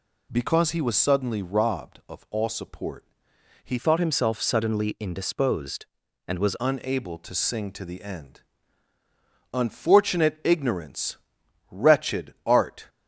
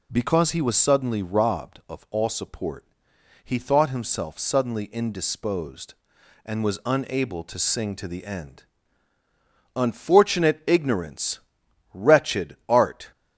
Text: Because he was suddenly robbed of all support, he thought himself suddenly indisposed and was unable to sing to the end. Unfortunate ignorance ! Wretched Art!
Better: second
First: changes voice from "thought" to "was"; from 3.7 to 6.5 s; 2.8 s long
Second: none

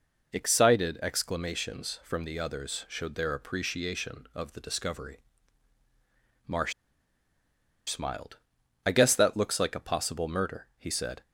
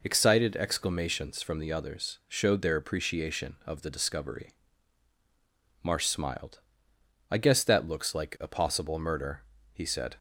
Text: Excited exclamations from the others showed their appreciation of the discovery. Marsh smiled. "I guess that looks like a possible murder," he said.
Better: second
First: pauses between "Marsh" and "smiled"; at 6.7 s; 1.1 s long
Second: none

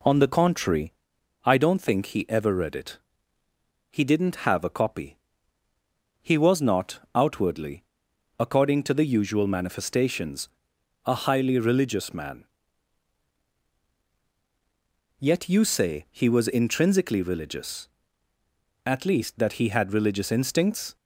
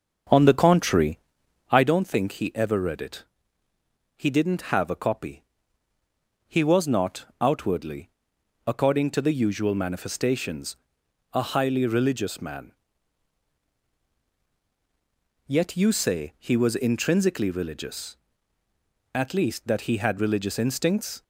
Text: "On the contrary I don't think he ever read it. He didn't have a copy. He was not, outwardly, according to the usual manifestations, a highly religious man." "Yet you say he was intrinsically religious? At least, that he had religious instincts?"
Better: first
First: pauses between "contrary" and "I"; noticeable; at 0.9 s; 0.52 s long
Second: starts louder than the rest; until 1.8 s; 7 dB // pauses between "contrary" and "I"; noticeable; at 1.1 s; 0.52 s long

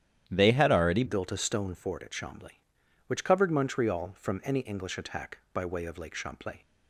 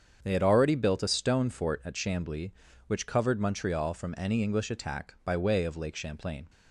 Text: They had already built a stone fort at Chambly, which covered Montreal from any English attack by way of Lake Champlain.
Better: second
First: starts louder than the rest; strong; until 1.3 s; 10 dB // changes voice at "built"; from 1.0 s on; 5.5 s long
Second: starts louder than the rest; strong; until 1.2 s; 7.5 dB

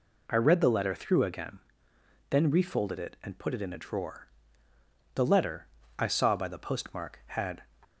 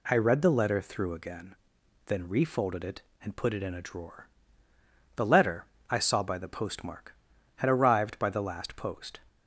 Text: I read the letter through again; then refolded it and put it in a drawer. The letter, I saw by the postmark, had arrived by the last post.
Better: second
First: stops before "arrived by the last post"; at 7.8 s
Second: none

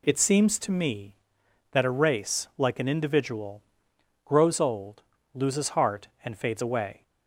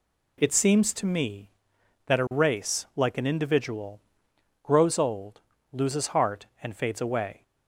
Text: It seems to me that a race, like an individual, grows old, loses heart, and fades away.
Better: neither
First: none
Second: none

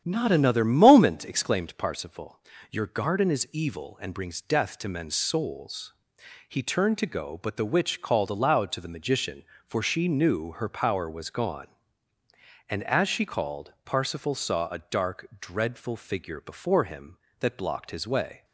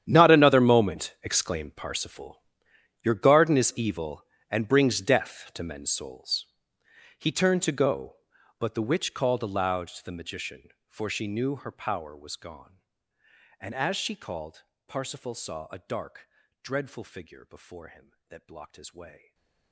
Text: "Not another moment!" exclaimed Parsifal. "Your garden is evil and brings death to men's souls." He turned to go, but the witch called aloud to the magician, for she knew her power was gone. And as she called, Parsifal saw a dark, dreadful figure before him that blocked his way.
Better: first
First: starts louder than the rest; strong; until 1.0 s; 9.5 dB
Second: gets quieter; strong; throughout; 19.5 dB // starts louder than the rest; strong; until 1.0 s; 10 dB // stays silent after the last word; slight; from 19.1 s on; 0.6 s long

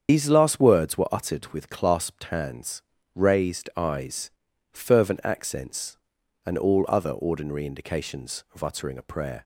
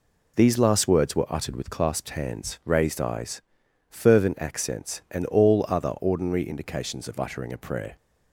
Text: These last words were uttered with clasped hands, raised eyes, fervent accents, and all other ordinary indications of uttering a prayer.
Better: second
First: loses the start of "These"; at 0.0 s; 70 ms // starts louder than the rest; strong; until 1.1 s; 7.5 dB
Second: none

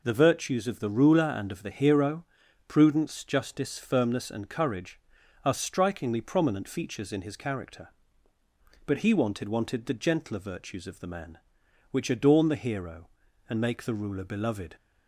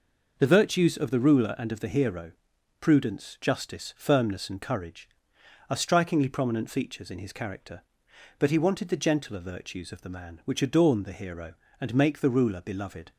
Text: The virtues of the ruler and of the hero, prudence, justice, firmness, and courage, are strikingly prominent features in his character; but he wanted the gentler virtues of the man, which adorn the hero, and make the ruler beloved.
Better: second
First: says "wanted" twice; at 9.4 s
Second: none

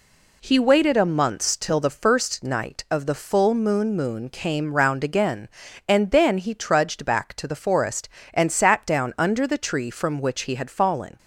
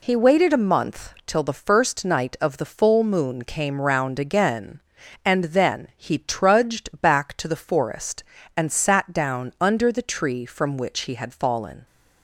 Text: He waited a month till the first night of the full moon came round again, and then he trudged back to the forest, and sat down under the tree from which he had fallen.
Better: second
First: says "moon" twice; at 3.9 s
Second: none

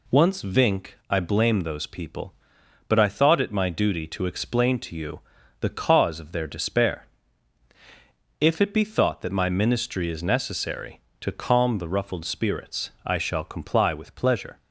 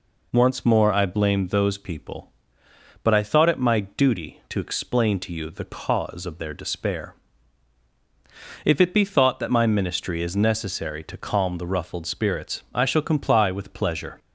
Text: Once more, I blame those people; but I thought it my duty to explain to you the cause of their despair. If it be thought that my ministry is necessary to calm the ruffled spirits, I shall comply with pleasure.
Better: second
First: says "vink" for "more"; at 0.4 s // pauses between "you" and "the"; at 5.1 s; 0.40 s long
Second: none

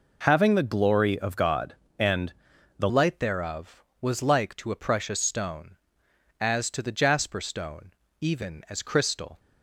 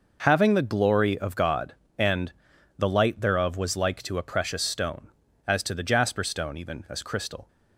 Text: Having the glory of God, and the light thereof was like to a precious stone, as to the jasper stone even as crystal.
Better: second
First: pauses between "and" and "the"; noticeable; at 2.3 s; 0.46 s long // changes voice at "light"; from 2.8 s on; 6.5 s long // pauses between "stone" and "even"; slight; at 7.9 s; 0.30 s long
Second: pauses between "and" and "the"; noticeable; at 2.3 s; 0.46 s long

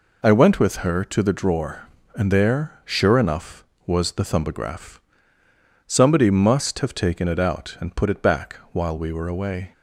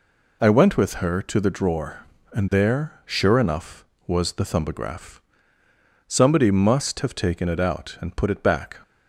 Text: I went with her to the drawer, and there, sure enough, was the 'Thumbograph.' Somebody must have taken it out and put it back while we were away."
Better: first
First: none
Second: stops before "while we were away"; at 8.8 s

